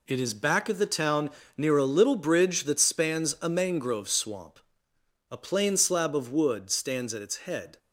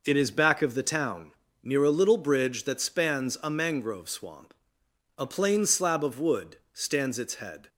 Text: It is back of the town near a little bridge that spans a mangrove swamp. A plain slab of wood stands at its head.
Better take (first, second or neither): first